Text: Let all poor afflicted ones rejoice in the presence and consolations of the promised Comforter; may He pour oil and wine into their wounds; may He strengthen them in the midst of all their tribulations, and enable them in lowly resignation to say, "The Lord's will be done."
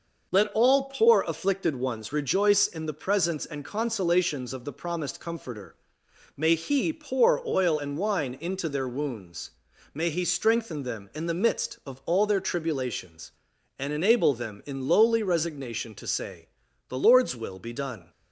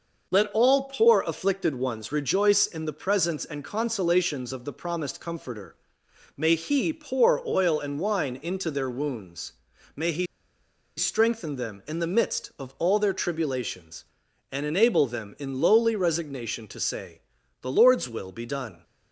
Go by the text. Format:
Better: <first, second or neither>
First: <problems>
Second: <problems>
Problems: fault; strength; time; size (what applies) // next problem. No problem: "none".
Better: first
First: none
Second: pauses between "He" and "strengthen"; noticeable; at 10.2 s; 0.71 s long